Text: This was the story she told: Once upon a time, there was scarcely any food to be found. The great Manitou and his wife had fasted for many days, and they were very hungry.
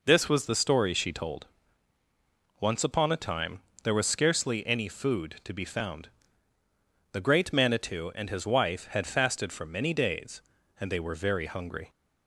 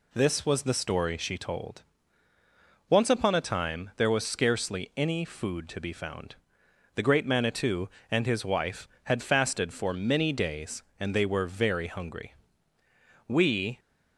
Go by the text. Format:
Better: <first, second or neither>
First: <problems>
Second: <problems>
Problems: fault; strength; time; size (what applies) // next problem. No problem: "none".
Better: first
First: none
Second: goes on to say "We"; from 13.2 s on; 0.50 s long